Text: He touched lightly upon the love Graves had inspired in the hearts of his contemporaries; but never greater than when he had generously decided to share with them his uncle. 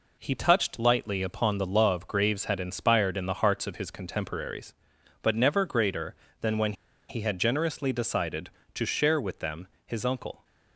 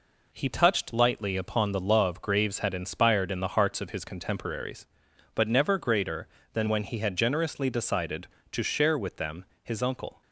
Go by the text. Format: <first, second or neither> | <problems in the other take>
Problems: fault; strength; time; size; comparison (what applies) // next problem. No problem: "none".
second | pauses between "when" and "he"; at 6.7 s; 0.36 s long // pauses between "them" and "his"; slight; at 9.6 s; 0.20 s long; slight in the second